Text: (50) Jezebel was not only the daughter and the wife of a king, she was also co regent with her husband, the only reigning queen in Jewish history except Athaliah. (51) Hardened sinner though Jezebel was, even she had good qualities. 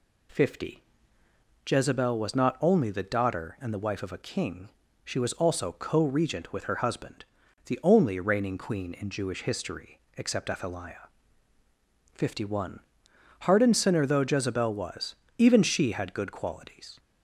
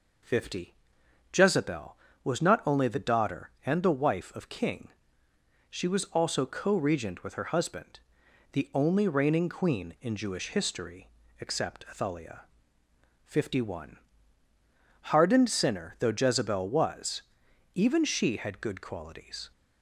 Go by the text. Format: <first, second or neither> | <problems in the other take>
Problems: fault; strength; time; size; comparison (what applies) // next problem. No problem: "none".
first | skips "a"; at 4.4 s // pauses between "history" and "except"; slight; at 11.0 s; 0.30 s long; slight in the first